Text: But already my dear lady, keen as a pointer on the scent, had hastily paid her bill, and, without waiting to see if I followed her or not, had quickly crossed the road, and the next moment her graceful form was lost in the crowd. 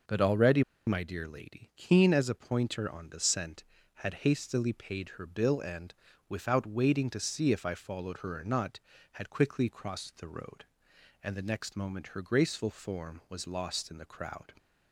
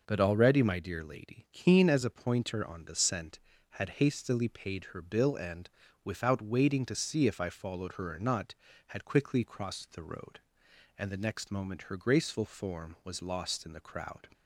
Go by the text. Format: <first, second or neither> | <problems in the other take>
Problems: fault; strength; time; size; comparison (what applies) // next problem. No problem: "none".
second | pauses between "already" and "my"; slight; at 0.6 s; 0.25 s long